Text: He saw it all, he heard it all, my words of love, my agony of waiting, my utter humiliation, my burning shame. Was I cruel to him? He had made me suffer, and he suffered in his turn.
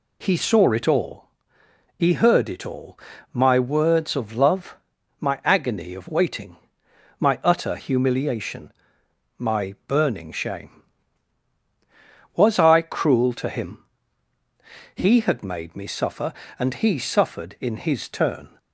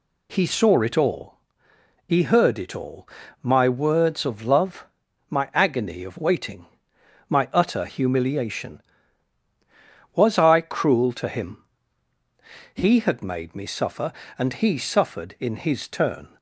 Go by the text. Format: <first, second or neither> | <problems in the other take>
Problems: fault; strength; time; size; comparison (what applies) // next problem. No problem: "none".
first | skips "my burning shame"; at 9.4 s